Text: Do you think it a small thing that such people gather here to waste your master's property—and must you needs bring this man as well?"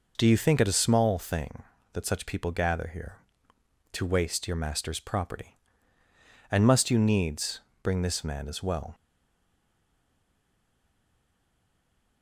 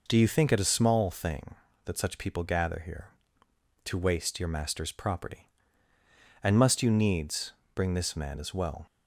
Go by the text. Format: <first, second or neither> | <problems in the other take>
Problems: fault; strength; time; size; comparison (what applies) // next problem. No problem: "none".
second | pauses between "needs" and "bring"; slight; at 7.5 s; 0.24 s long; slight in the second // stays silent after the last word; strong; from 8.9 s on; 3.3 s long